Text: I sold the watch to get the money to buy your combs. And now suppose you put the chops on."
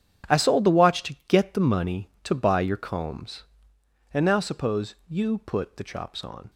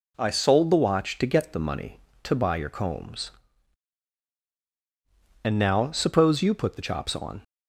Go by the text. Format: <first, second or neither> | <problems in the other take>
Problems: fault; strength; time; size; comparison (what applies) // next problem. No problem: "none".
second | gets quieter; strong; throughout; 15 dB